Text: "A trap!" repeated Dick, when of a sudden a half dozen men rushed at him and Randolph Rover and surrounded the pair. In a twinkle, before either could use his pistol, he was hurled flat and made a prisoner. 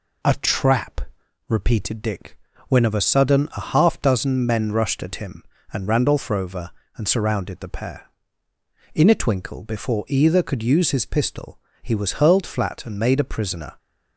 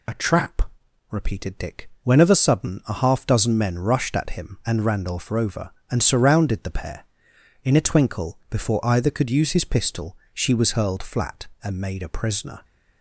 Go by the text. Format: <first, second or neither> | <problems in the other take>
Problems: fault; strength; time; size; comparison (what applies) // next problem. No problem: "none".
first | says "she" for "he"; at 10.3 s